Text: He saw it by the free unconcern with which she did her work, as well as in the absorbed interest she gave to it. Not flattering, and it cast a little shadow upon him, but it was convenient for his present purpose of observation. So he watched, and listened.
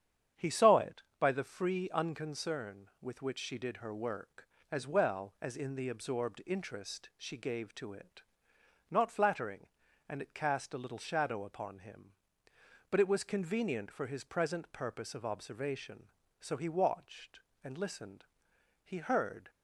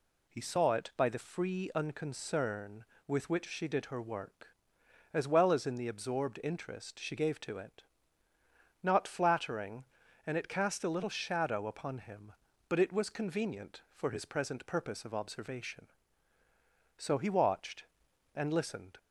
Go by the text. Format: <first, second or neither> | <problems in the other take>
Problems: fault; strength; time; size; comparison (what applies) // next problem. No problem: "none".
second | starts louder than the rest; strong; until 1.5 s; 8.5 dB // goes on to say "He heard"; noticeable; from 18.8 s on; 0.66 s long